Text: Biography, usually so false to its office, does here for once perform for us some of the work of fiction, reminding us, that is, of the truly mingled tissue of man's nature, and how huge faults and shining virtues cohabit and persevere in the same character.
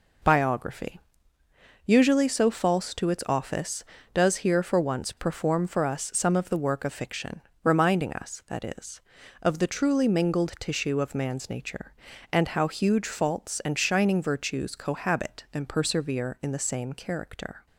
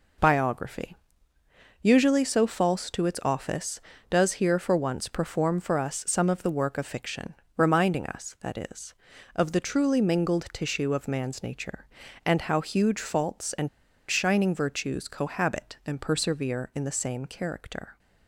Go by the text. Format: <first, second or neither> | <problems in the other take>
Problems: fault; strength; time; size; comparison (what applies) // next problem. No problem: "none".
first | pauses between "and" and "shining"; at 13.6 s; 0.41 s long